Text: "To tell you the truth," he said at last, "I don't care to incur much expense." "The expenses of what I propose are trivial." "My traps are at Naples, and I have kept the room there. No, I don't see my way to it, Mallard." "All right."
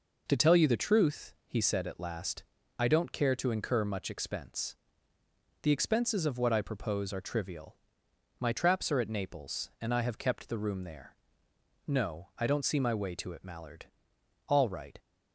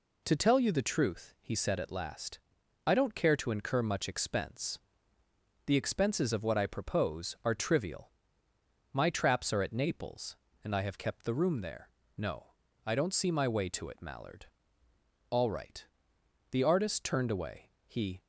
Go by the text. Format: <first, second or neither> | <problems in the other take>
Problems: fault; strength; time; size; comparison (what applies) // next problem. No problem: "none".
first | goes on to say "The artist turned away He"; strong; from 16.5 s on; 1.7 s long